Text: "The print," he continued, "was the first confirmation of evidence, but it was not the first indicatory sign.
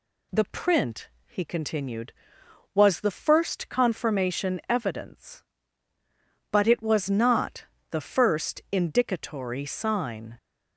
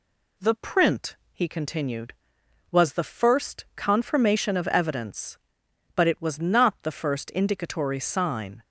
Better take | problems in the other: second | skips "of"; at 4.6 s // pauses between "not" and "the"; slight; at 7.6 s; 0.24 s long

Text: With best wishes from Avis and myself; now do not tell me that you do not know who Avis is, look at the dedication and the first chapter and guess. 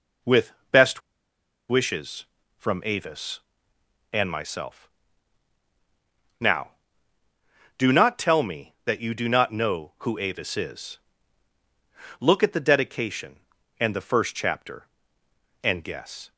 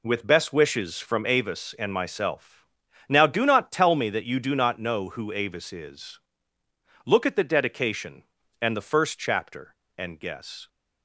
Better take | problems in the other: second | pauses between "With" and "best"; slight; at 0.5 s; 0.18 s long // pauses between "best" and "wishes"; noticeable; at 1.0 s; 0.69 s long

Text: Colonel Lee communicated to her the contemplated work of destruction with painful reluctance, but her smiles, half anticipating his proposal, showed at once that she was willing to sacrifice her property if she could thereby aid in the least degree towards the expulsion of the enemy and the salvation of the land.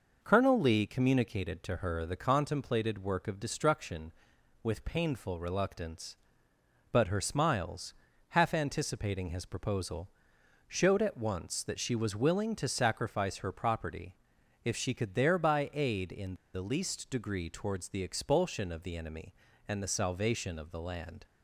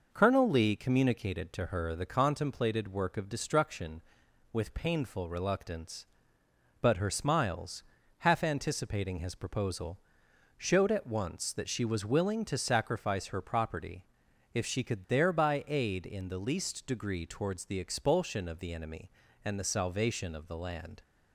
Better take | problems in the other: second | pauses between "property" and "if"; noticeable; at 14.1 s; 0.50 s long; noticeable in the second // pauses between "in" and "the"; slight; at 16.3 s; 0.18 s long

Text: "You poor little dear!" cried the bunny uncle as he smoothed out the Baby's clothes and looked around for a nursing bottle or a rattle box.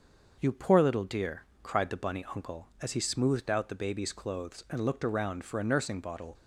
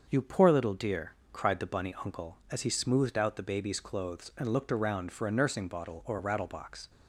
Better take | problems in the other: second | starts louder than the rest; until 1.4 s; 6.5 dB; also in the second // stops before "or a rattle box"; at 6.3 s

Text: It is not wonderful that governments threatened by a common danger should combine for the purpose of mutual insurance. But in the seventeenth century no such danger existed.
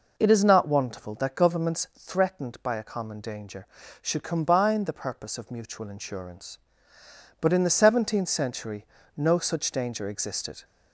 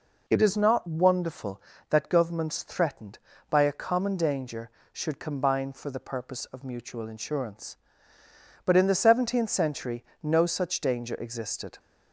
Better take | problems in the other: second | skips "for"; at 4.8 s // pauses between "century" and "no"; slight; at 8.8 s; 0.28 s long; slight in the second

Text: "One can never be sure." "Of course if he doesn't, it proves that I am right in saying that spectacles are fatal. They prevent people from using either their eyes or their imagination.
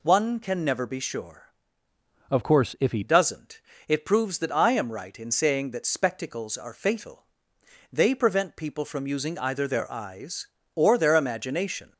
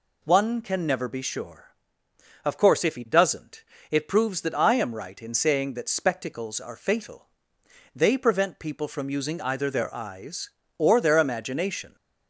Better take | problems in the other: second | changes voice from "Of" to "he"; from 2.2 to 3.0 s; 0.8 s long

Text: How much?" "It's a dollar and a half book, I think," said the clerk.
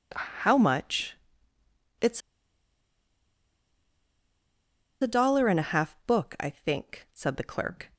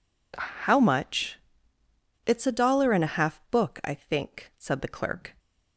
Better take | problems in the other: second | pauses between "It's" and "a"; strong; at 2.2 s; 2.8 s long

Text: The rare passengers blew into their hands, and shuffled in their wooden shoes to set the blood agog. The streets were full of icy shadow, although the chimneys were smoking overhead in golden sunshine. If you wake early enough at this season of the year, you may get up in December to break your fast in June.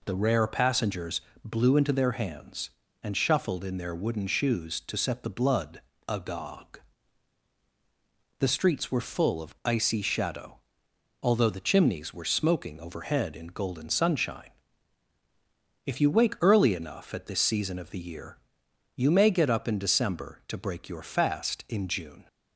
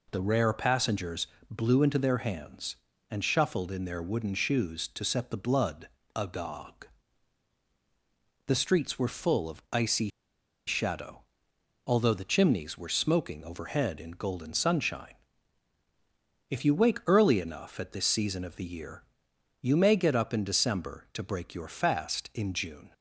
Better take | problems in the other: first | pauses between "passengers" and "blew"; slight; at 1.2 s; 0.24 s long; slight in the first // pauses between "blood" and "agog"; slight; at 5.8 s; 0.28 s long; slight in the first // pauses between "icy" and "shadow"; noticeable; at 10.0 s; 0.58 s long

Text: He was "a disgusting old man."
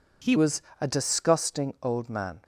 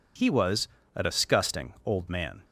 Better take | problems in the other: second | changes voice at "was"; from 0.3 s on; 2.1 s long // pauses between "was" and "a"; slight; at 0.6 s; 0.20 s long; slight in the second

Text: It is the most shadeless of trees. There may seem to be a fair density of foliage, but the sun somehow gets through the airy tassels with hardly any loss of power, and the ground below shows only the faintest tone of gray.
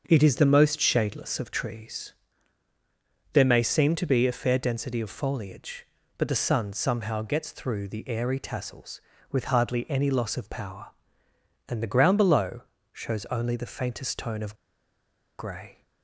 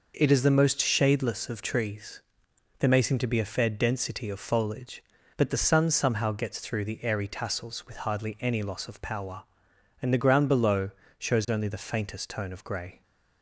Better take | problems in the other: second | starts louder than the rest; until 1.0 s; 6.5 dB // pauses between "below" and "shows"; slight; at 12.6 s; 0.30 s long; slight in the second // pauses between "of" and "gray"; noticeable; at 14.5 s; 0.85 s long

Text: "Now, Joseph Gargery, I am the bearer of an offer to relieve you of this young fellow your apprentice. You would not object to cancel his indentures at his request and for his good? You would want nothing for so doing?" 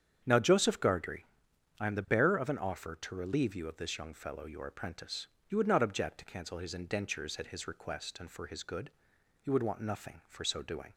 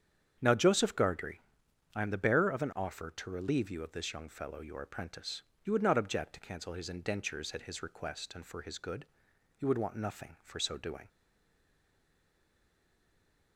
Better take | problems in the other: first | starts louder than the rest; strong; until 1.4 s; 8 dB; strong in the first // stays silent after the last word; from 11.0 s on; 2.5 s long

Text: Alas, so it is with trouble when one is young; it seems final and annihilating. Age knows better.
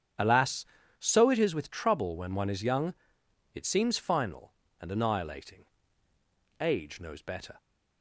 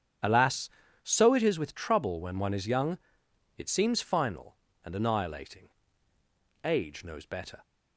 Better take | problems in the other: neither | starts louder than the rest; strong; the same in both

